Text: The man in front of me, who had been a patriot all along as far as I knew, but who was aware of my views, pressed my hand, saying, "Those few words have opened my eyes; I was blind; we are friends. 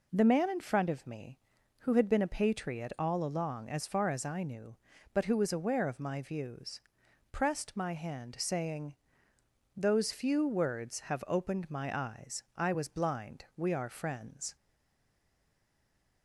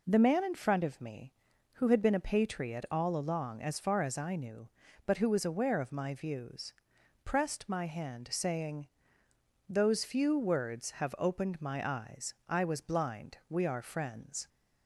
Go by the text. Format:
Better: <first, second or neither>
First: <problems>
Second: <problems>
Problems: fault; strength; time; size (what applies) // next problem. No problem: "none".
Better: second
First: stays silent after the last word; noticeable; from 14.5 s on; 1.7 s long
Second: none